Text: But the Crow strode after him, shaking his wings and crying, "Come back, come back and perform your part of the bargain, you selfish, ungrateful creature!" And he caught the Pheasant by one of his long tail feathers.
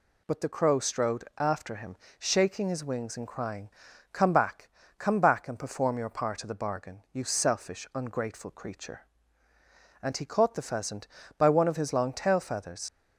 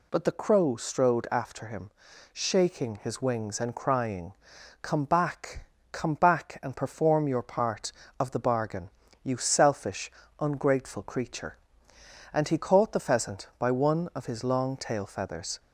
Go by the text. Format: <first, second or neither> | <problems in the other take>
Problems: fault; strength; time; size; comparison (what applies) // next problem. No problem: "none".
second | leaves "feathers" unfinished; at 12.8 s; 70 ms